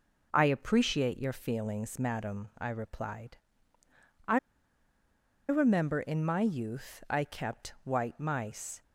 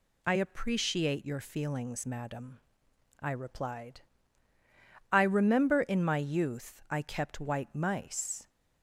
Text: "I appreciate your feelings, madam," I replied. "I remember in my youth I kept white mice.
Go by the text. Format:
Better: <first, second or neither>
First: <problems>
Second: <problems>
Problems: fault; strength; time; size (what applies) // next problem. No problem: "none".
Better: second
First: pauses between "I" and "remember"; at 4.3 s; 1.1 s long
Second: none